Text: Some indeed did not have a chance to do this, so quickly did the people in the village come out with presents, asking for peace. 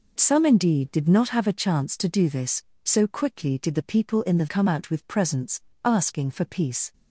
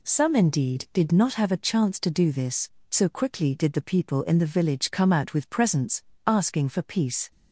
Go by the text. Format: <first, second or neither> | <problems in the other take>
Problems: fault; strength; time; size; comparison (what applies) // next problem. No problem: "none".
second | skips "village"; at 4.4 s